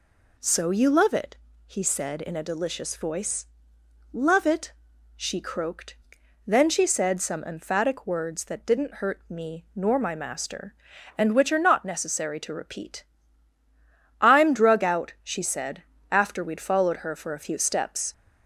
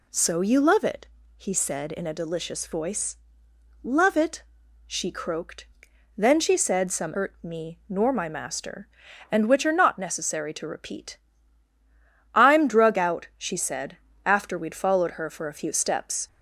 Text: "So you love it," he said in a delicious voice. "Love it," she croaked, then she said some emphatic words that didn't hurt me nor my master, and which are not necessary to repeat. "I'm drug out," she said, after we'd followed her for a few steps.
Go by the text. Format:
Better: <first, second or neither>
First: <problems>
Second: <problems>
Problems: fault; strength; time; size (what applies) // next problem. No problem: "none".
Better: first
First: none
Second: skips "emphatic words that didn't"; at 7.1 s